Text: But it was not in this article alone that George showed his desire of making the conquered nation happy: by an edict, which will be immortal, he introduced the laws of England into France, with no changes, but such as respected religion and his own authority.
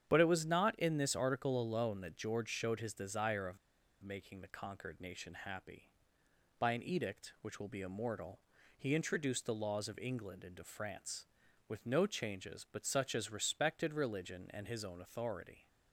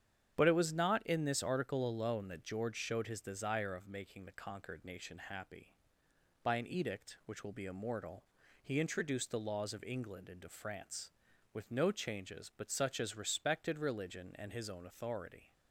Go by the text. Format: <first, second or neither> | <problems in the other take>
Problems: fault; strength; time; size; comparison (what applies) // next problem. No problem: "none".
second | starts louder than the rest; strong; until 1.1 s; 8.5 dB; strong in the second // pauses between "of" and "making"; at 3.5 s; 0.45 s long